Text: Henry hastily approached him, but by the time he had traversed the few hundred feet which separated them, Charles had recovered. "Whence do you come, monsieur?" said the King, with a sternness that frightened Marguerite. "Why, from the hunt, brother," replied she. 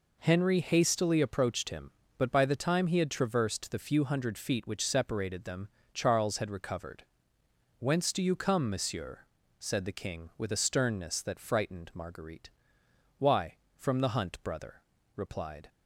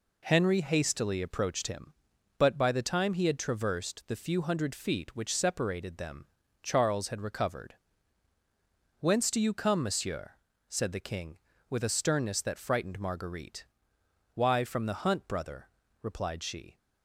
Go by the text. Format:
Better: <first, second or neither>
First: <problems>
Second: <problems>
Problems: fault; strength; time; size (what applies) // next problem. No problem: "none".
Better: second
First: stops before "she"; at 15.6 s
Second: none